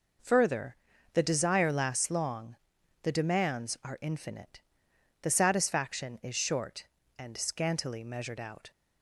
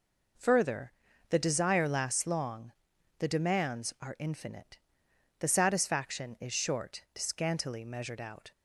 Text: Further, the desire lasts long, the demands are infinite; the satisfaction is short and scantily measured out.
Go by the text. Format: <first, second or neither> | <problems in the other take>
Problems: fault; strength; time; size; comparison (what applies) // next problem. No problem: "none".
first | skips "and"; at 7.1 s